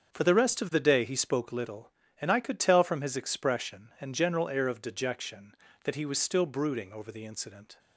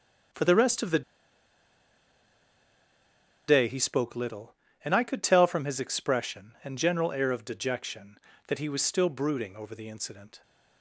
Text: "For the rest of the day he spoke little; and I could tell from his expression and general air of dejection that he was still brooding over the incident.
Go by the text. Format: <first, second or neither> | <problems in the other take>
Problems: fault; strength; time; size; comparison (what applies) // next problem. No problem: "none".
first | starts louder than the rest; until 3.8 s; 7 dB; also in the first // pauses between "the" and "day"; strong; at 1.0 s; 2.4 s long